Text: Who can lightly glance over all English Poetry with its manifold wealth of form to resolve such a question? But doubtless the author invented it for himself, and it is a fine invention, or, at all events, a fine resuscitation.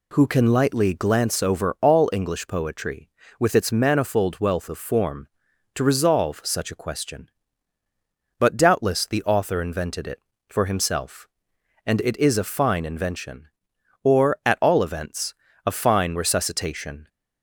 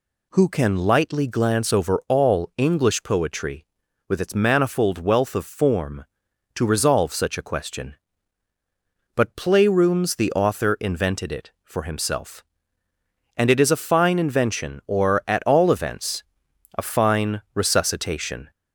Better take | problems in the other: first | says "playrooms" for "doubtless"; at 9.3 s

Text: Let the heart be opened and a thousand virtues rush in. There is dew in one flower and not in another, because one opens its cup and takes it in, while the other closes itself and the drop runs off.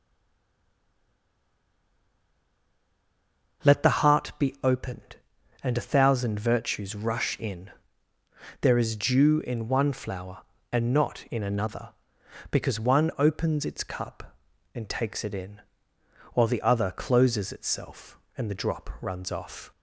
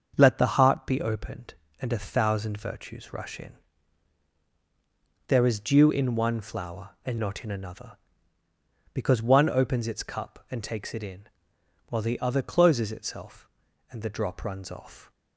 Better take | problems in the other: second | stays silent before the first word; strong; until 3.6 s; 3.6 s long // starts louder than the rest; until 4.8 s; 6.5 dB; also in the second

